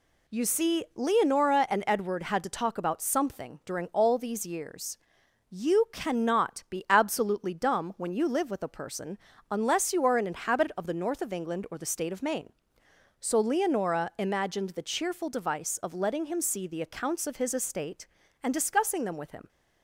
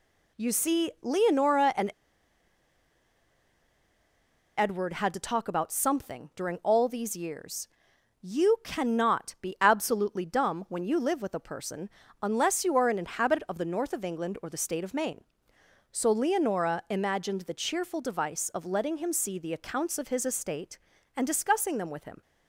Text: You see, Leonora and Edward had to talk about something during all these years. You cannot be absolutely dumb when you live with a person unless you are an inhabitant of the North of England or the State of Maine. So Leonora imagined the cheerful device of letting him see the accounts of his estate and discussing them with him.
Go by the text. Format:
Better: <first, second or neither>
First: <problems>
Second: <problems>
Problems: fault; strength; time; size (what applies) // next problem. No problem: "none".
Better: first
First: pauses between "person" and "unless"; slight; at 9.1 s; 0.32 s long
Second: pauses between "and" and "Edward"; strong; at 1.9 s; 2.6 s long // pauses between "person" and "unless"; slight; at 11.9 s; 0.32 s long